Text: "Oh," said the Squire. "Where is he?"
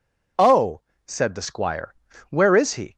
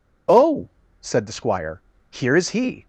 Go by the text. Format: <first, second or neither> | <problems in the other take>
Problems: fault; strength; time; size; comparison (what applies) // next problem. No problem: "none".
first | says "Here" for "Where"; at 2.1 s